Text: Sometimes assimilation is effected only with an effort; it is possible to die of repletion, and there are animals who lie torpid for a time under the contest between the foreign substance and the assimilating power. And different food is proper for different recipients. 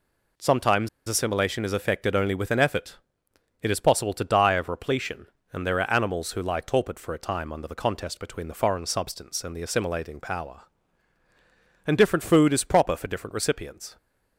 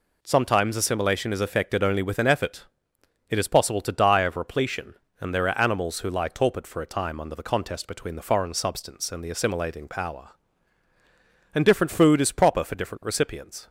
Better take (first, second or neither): second